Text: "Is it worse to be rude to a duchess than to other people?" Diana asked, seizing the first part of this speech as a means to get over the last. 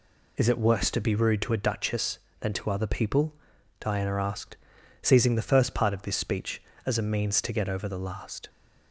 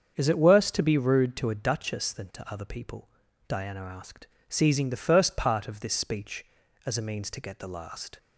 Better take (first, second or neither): first